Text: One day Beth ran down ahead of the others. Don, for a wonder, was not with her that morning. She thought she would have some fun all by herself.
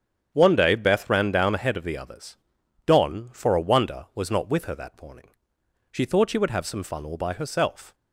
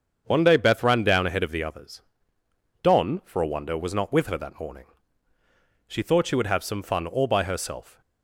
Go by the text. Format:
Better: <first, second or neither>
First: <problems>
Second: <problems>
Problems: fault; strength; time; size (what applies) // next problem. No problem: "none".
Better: neither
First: starts louder than the rest; strong; until 1.3 s; 8.5 dB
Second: starts louder than the rest; until 1.2 s; 7 dB